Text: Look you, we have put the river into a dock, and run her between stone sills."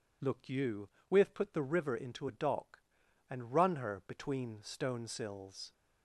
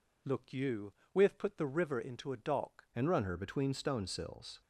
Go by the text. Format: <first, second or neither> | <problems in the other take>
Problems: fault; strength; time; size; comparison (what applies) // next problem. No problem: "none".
first | changes voice at "and"; from 2.9 s on; 1.7 s long